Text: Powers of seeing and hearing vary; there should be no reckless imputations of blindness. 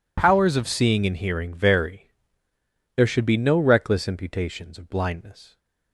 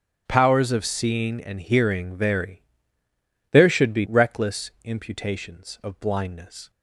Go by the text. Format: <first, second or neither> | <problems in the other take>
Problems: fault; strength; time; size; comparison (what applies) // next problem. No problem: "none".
first | starts louder than the rest; until 1.2 s; 6.5 dB // skips "no"; at 4.0 s